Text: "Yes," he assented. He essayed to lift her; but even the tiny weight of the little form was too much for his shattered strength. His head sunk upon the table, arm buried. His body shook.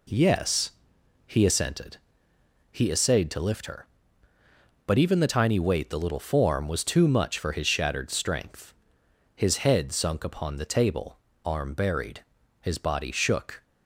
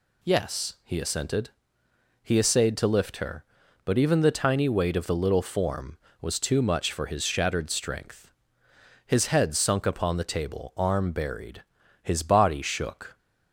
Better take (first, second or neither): second